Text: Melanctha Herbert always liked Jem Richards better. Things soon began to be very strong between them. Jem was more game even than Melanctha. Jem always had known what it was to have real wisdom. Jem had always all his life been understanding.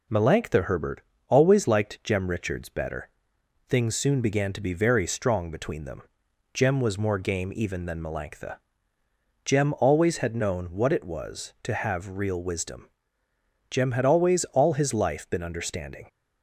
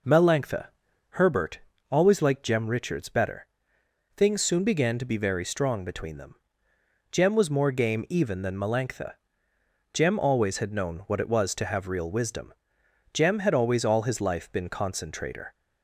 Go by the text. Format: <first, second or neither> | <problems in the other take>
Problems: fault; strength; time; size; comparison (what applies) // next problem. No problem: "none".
first | pauses between "Melanctha" and "Herbert"; at 0.6 s; 0.42 s long // pauses between "Herbert" and "always"; slight; at 1.5 s; 0.32 s long; slight in the first // says "concentrator" for "understanding"; at 14.6 s